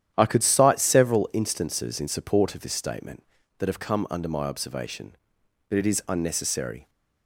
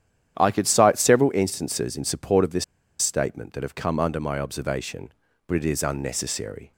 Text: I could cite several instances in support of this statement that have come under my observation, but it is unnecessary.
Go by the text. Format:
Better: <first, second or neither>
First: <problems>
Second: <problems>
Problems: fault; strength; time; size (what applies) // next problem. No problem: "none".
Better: first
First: starts louder than the rest; strong; until 1.1 s; 10.5 dB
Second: starts louder than the rest; strong; until 1.3 s; 10 dB // pauses between "this" and "statement"; slight; at 2.6 s; 0.35 s long